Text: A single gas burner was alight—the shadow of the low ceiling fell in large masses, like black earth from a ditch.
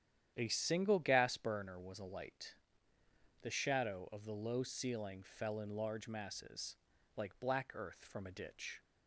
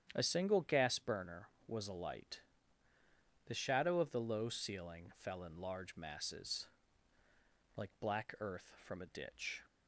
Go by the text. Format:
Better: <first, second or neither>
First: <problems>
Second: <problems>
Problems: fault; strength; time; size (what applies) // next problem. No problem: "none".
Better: neither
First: starts louder than the rest; strong; until 1.3 s; 10 dB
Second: starts louder than the rest; strong; until 1.1 s; 9 dB